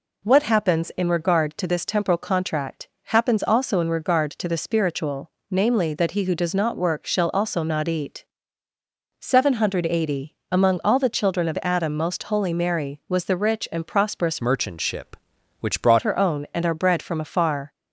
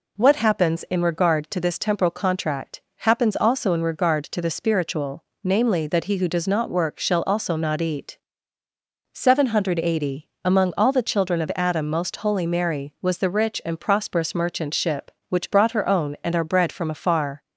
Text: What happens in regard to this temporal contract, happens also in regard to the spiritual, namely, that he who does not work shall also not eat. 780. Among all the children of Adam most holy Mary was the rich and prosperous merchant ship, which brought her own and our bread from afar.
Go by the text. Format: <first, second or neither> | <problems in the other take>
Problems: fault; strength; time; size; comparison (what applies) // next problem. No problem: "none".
second | changes voice from "merchant" to "brought"; from 14.4 to 16.0 s; 1.6 s long